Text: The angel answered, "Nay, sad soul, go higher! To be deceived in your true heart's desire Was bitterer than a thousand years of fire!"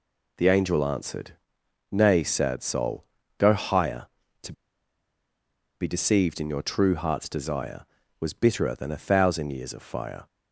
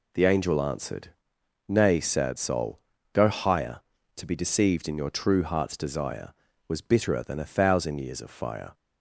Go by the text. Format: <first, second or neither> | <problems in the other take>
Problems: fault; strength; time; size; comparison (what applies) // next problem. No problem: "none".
second | pauses between "To" and "be"; strong; at 4.5 s; 1.2 s long